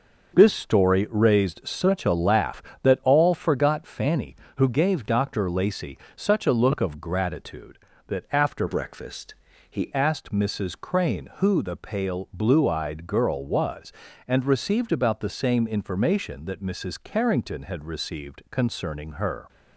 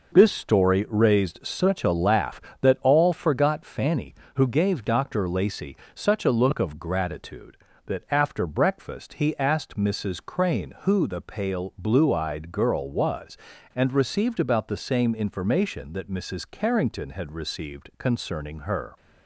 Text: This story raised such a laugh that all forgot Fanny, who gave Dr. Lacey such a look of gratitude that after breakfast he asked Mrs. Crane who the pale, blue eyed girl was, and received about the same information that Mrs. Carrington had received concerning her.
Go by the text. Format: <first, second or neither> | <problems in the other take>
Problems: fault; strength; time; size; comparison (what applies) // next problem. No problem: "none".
second | starts louder than the rest; noticeable; until 1.3 s; 6 dB // pauses between "Lacey" and "such"; slight; at 5.9 s; 0.20 s long; slight in the second // changes voice from "breakfast" to "he"; from 8.6 to 9.9 s; 1.3 s long // pauses between "breakfast" and "he"; slight; at 9.3 s; 0.34 s long